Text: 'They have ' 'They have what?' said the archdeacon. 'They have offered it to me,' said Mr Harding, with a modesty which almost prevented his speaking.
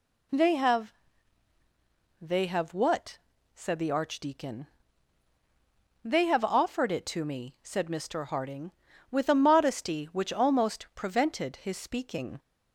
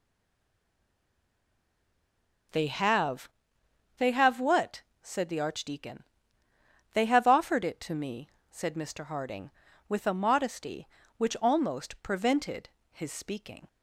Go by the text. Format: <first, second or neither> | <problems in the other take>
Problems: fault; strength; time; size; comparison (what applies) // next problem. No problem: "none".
first | stays silent before the first word; until 2.5 s; 2.5 s long // pauses between "prevented" and "his"; slight; at 12.6 s; 0.22 s long